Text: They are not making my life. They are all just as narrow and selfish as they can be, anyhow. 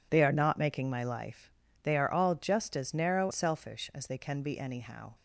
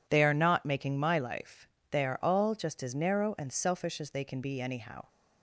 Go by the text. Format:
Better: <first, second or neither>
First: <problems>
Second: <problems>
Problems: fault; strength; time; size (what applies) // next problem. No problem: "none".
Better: second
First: skips "and"; at 3.3 s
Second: none